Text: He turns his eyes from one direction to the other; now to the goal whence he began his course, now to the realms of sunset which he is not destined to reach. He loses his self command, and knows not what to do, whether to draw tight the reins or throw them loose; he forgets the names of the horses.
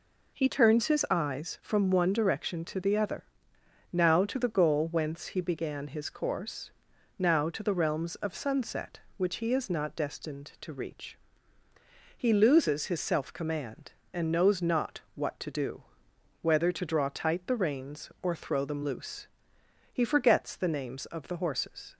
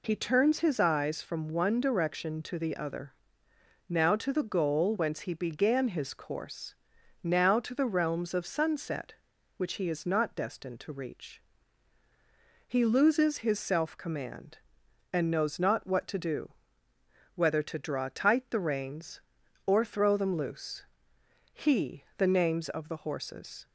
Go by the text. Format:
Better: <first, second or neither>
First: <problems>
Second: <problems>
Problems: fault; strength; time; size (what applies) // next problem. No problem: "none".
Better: first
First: none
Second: skips "forgets"; at 22.1 s